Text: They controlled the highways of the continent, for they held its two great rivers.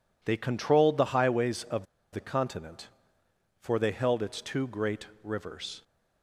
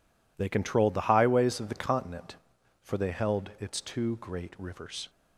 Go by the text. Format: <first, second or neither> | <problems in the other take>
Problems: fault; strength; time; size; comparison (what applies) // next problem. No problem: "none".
second | pauses between "of" and "the"; slight; at 1.8 s; 0.27 s long // pauses between "great" and "rivers"; slight; at 5.0 s; 0.16 s long